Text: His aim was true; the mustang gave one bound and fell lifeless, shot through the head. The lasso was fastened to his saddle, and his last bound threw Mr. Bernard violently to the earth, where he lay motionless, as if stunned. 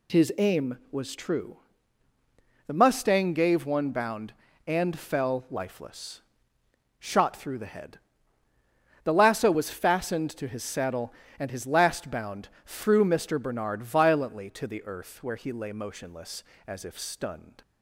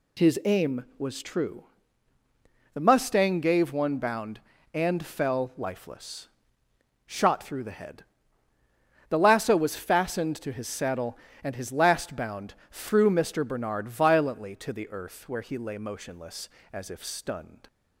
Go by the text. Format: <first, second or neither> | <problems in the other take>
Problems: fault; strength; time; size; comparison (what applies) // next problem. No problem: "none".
neither | pauses between "bound" and "threw"; slight; the same in both